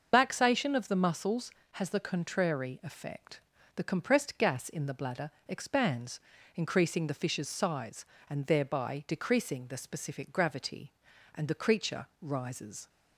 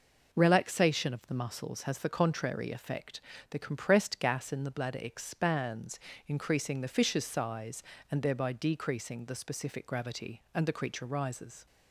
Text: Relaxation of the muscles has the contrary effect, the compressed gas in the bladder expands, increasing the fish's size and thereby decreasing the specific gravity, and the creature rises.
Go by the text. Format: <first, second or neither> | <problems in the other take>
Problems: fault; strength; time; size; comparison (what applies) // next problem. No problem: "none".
second | loses the start of "Relaxation"; at 0.1 s; 145 ms // starts louder than the rest; noticeable; until 1.1 s; 6 dB // pauses between "bladder" and "expands"; slight; at 5.3 s; 0.18 s long // pauses between "creature" and "rises"; slight; at 12.0 s; 0.16 s long